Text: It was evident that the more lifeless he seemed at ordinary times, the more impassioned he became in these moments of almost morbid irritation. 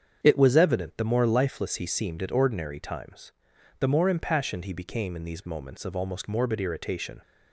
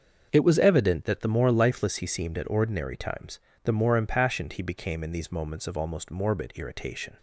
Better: second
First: starts louder than the rest; strong; until 1.2 s; 7.5 dB // skips "that"; at 0.9 s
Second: starts louder than the rest; until 1.3 s; 6.5 dB

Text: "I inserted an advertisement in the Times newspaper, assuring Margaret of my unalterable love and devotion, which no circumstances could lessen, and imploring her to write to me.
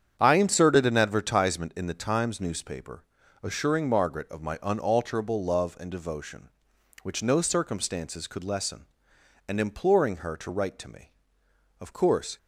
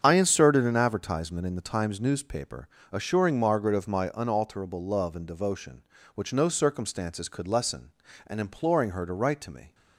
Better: second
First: starts louder than the rest; strong; until 1.2 s; 8.5 dB // goes on to say "Of course"; from 11.8 s on; 0.56 s long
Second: starts louder than the rest; strong; until 1.0 s; 7.5 dB

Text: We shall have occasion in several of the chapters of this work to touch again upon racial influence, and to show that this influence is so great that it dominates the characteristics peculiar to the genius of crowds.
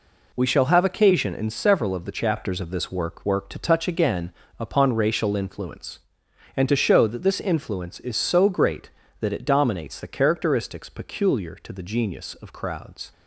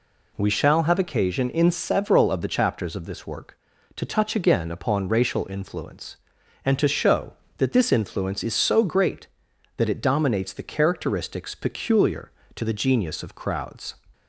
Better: second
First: says "work" twice; at 3.2 s // pauses between "again" and "upon"; slight; at 4.3 s; 0.28 s long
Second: none

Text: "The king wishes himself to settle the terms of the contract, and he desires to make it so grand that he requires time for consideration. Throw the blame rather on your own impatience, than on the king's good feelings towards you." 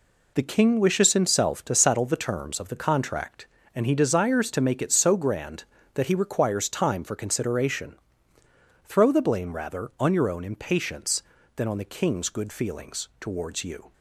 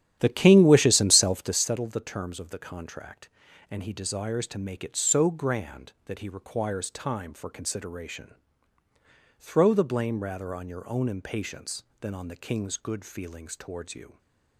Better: first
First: none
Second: starts louder than the rest; strong; until 1.6 s; 11 dB

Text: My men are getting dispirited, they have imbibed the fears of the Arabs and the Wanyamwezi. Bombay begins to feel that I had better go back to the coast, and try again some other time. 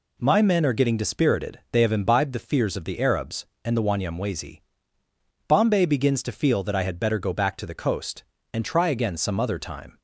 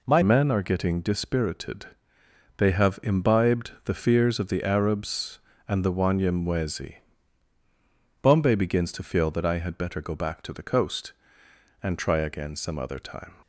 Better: first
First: none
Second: changes voice at "men"; from 0.2 s on; 13.1 s long

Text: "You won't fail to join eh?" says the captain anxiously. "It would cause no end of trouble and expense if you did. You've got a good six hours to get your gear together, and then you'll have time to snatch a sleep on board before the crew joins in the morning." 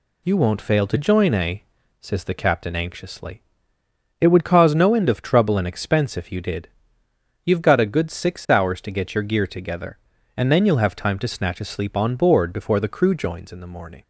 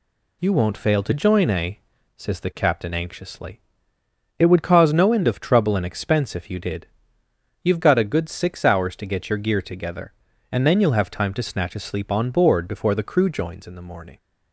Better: neither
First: none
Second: none

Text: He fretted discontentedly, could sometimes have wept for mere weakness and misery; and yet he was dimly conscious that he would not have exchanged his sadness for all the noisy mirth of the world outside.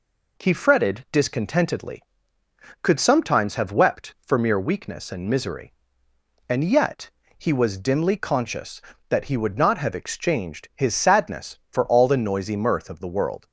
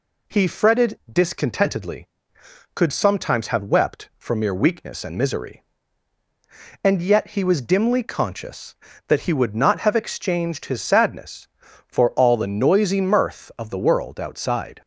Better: second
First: pauses between "yet" and "he"; slight; at 7.1 s; 0.28 s long // stops before "outside"; at 13.4 s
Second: none

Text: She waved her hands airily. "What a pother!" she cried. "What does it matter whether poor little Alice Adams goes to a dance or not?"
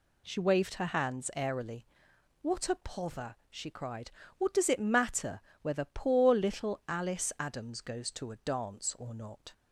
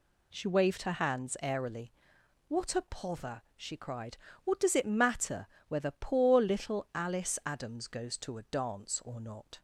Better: neither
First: pauses between "matter" and "whether"; slight; at 5.4 s; 0.18 s long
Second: pauses between "matter" and "whether"; slight; at 5.4 s; 0.18 s long

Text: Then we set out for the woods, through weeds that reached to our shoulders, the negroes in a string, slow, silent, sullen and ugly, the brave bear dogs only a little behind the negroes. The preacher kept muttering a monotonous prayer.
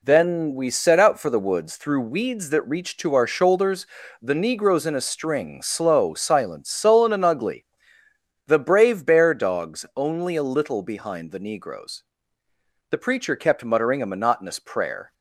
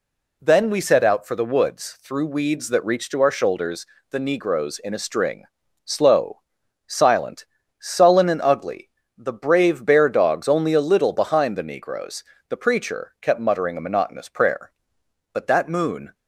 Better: first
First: none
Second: goes on to say "But that moon"; noticeable; from 15.3 s on; 0.80 s long

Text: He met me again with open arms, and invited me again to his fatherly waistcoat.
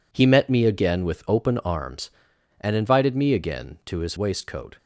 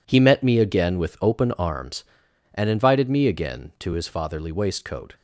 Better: second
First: skips "fatherly"; at 4.1 s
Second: none

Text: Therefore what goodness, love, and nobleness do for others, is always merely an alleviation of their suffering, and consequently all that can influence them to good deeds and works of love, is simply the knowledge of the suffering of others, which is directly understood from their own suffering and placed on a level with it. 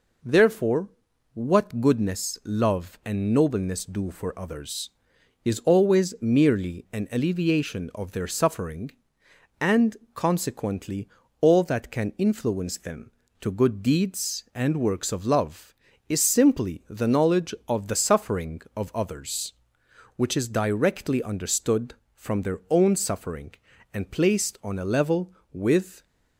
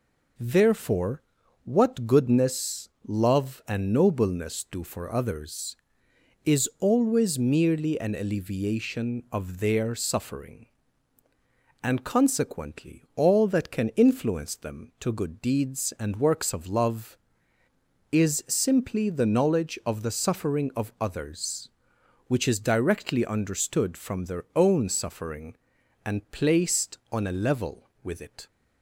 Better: second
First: pauses between "Therefore" and "what"; at 0.8 s; 0.44 s long // pauses between "and" and "consequently"; slight; at 9.9 s; 0.18 s long // pauses between "consequently" and "all"; slight; at 11.0 s; 0.32 s long // stops before "it"; at 26.0 s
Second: pauses between "Therefore" and "what"; at 1.2 s; 0.42 s long

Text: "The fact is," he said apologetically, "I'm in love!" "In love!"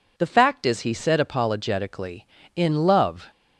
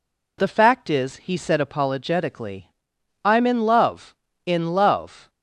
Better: second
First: skips "I'm in love"; at 2.4 s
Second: none

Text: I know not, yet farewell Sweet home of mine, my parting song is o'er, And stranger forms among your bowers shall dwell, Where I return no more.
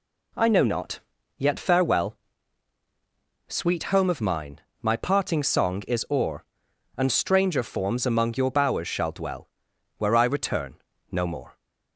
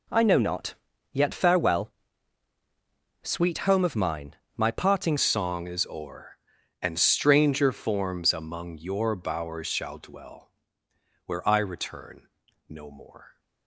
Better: first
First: pauses between "farewell" and "Sweet"; strong; at 2.1 s; 1.3 s long // pauses between "return" and "no"; slight; at 10.7 s; 0.34 s long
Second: pauses between "farewell" and "Sweet"; strong; at 1.9 s; 1.3 s long // changes voice at "song"; from 5.1 s on; 8.2 s long // pauses between "return" and "no"; at 12.2 s; 0.40 s long

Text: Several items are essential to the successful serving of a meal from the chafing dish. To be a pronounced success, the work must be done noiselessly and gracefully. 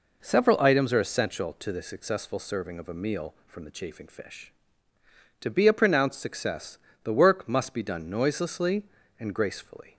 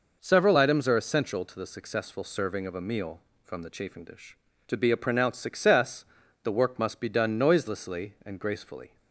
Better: second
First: says "fish" for "dish"; at 4.0 s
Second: none

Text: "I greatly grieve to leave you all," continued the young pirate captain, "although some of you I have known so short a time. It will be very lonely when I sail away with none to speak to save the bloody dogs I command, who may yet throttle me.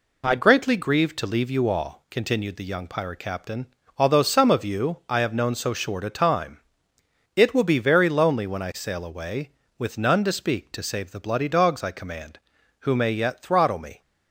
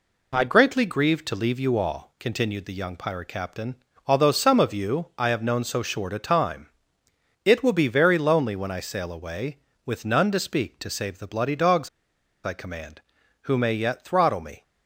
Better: first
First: none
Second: pauses between "dogs" and "I"; noticeable; at 11.8 s; 0.57 s long

